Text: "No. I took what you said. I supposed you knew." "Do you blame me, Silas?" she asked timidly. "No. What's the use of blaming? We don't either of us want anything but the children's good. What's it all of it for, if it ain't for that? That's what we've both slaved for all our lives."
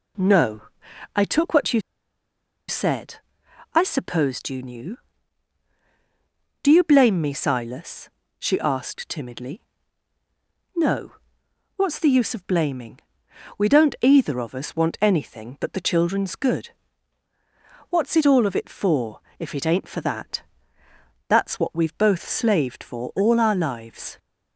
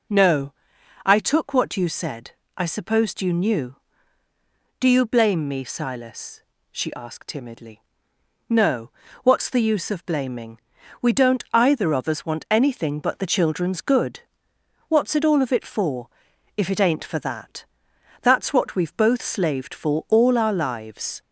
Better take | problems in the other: second | pauses between "you" and "said"; noticeable; at 1.8 s; 0.87 s long

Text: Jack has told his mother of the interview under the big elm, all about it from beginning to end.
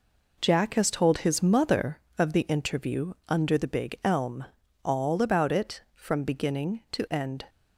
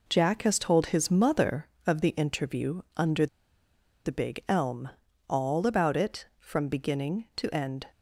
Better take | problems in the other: first | pauses between "under" and "the"; noticeable; at 3.2 s; 0.79 s long

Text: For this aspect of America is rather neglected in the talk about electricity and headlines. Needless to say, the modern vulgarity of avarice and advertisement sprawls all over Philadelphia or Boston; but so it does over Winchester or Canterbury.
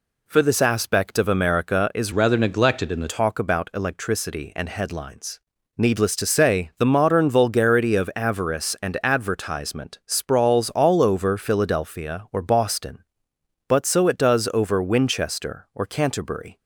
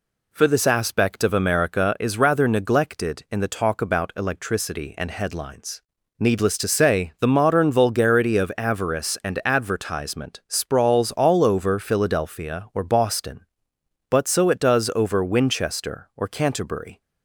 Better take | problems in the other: second | changes voice from "rather" to "the"; from 2.1 to 3.0 s; 0.9 s long

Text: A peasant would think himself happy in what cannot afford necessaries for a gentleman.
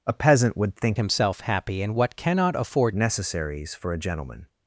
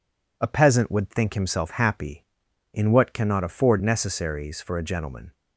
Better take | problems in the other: second | changes voice from "himself" to "afford"; from 0.9 to 2.9 s; 2.0 s long

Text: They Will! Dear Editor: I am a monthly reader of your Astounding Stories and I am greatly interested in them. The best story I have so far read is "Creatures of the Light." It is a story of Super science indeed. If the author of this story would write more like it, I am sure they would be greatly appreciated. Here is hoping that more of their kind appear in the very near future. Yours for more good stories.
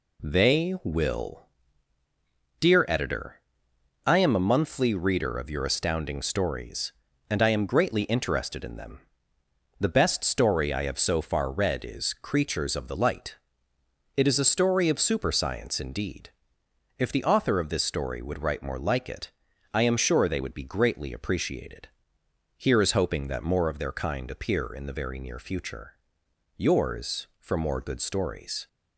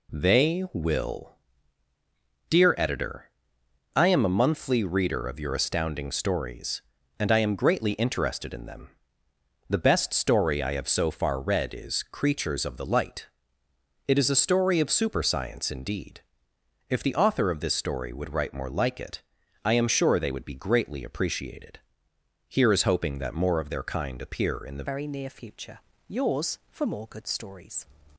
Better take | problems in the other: first | changes voice at "very"; from 24.8 s on; 3.0 s long

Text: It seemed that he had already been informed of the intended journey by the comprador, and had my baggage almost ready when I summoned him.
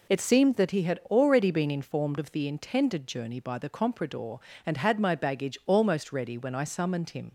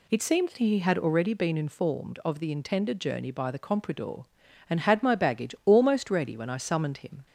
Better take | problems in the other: neither | none

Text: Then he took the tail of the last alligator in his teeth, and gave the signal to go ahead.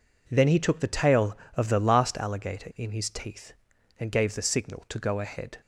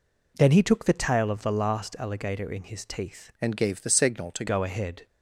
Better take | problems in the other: first | changes voice from "and" to "to"; from 3.4 to 4.4 s; 1.0 s long

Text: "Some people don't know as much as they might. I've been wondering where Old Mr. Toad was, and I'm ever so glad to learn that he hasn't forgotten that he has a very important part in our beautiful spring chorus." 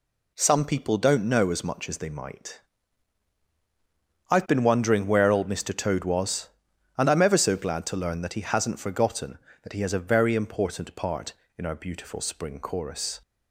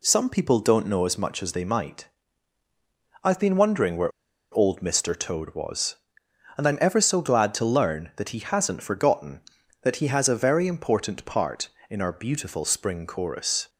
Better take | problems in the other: first | pauses between "where" and "Old"; at 4.1 s; 0.40 s long

